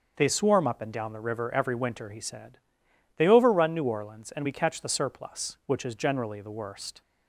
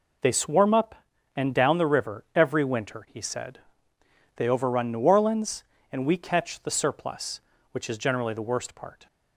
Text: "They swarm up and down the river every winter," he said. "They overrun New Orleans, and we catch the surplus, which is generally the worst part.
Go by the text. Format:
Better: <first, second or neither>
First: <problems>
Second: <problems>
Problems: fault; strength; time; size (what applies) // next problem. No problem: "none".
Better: second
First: starts louder than the rest; until 1.1 s; 6 dB // stops before "part"; at 7.0 s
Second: none